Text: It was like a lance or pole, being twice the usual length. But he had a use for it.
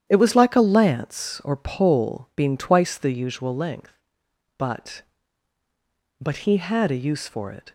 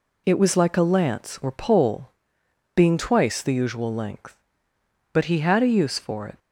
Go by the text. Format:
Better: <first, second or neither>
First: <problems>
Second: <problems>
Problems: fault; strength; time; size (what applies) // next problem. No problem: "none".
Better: second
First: starts louder than the rest; strong; until 1.0 s; 10 dB // says "But" twice; at 6.2 s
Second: none